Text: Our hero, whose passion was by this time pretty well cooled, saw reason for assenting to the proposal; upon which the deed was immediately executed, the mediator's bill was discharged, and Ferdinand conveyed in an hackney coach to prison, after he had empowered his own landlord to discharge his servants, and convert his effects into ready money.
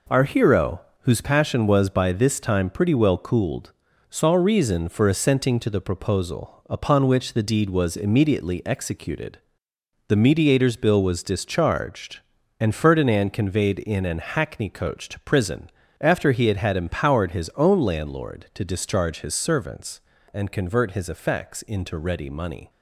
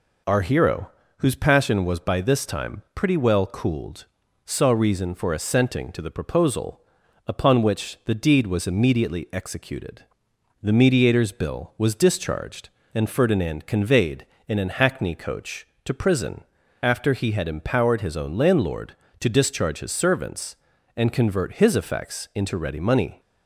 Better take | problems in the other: second | says "had" twice; at 16.5 s

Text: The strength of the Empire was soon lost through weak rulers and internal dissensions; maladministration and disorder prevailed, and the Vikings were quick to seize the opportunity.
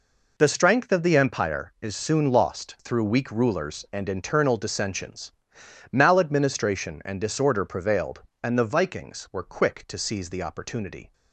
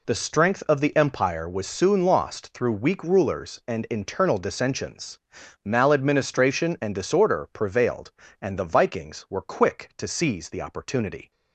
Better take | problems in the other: second | says "is" for "was"; at 1.8 s

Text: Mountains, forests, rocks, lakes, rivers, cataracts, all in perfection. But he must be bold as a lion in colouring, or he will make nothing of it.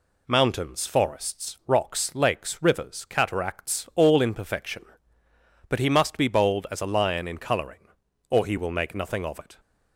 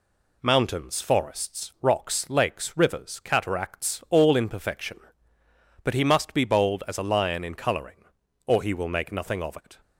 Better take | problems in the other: neither | none

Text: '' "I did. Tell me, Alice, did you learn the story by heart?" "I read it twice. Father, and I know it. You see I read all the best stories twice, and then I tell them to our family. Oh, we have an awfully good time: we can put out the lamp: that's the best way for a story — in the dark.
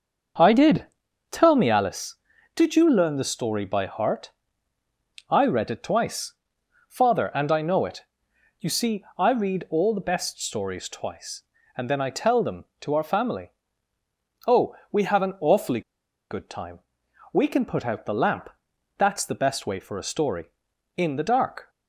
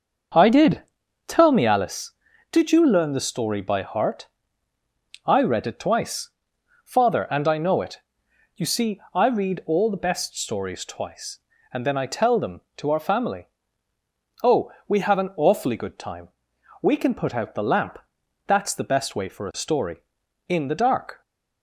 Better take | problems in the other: second | starts louder than the rest; until 1.8 s; 6.5 dB; also in the second // pauses between "awfully" and "good"; noticeable; at 15.8 s; 0.49 s long

